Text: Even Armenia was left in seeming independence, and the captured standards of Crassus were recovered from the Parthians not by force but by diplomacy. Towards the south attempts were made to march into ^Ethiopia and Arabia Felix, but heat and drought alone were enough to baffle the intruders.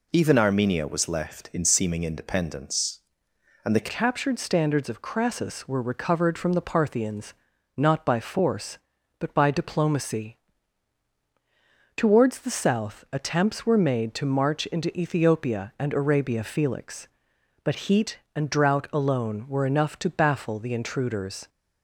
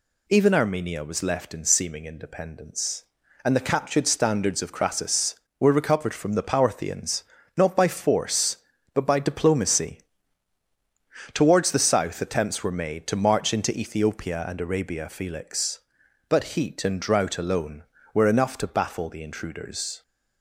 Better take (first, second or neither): second